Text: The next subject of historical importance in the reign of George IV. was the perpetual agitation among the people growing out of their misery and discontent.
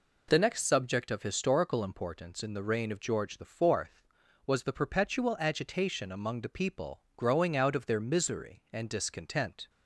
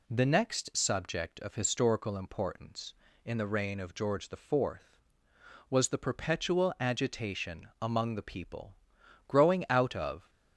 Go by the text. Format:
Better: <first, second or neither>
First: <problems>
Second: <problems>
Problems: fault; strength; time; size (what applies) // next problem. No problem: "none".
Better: first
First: none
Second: pauses between "people" and "growing"; noticeable; at 8.7 s; 0.52 s long // stops before "their misery and discontent"; at 10.2 s